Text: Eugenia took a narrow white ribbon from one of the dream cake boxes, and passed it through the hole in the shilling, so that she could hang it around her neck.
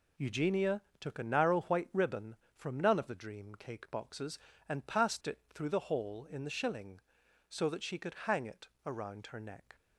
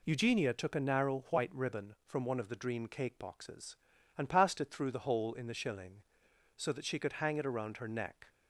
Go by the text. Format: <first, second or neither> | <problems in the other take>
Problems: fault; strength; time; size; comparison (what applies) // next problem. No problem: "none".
second | pauses between "Eugenia" and "took"; slight; at 0.8 s; 0.18 s long // says "none" for "one"; at 2.7 s // pauses between "it" and "around"; slight; at 8.6 s; 0.16 s long